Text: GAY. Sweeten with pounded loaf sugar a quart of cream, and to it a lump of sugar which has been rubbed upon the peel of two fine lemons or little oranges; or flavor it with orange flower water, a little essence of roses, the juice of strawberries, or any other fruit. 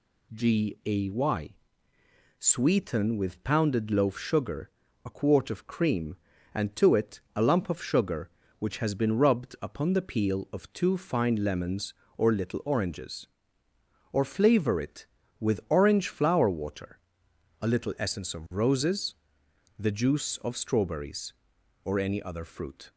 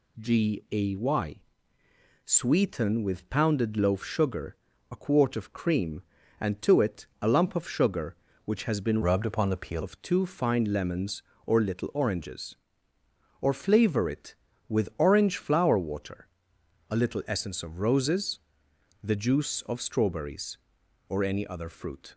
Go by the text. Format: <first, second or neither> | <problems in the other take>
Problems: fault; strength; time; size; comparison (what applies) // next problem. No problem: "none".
first | pauses between "sugar" and "a"; at 4.5 s; 0.38 s long; also in the first // changes voice from "rubbed" to "peel"; from 9.0 to 9.8 s; 0.8 s long